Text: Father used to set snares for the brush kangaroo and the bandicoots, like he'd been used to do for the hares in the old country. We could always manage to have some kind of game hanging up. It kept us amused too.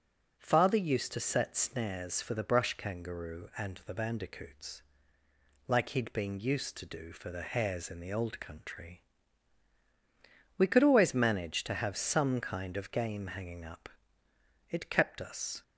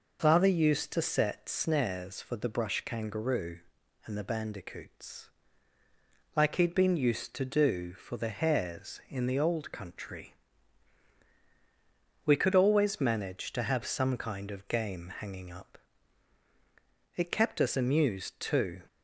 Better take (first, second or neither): second